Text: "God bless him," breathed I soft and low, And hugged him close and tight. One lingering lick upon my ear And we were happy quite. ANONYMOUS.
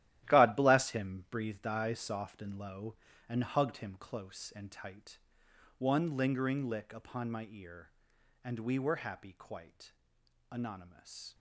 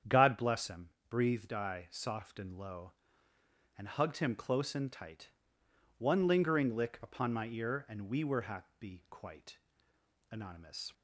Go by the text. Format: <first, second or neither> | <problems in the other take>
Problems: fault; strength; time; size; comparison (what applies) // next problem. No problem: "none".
second | gets quieter; strong; throughout; 10.5 dB // starts louder than the rest; strong; until 1.3 s; 13.5 dB; strong in the second